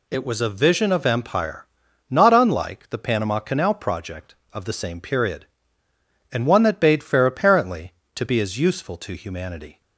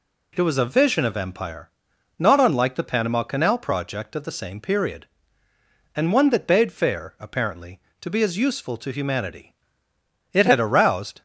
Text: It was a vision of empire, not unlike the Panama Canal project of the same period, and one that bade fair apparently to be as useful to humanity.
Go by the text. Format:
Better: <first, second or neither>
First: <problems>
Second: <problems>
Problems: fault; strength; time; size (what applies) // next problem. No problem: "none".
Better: first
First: none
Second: goes on to say "It had aroused"; noticeable; from 10.3 s on; 0.90 s long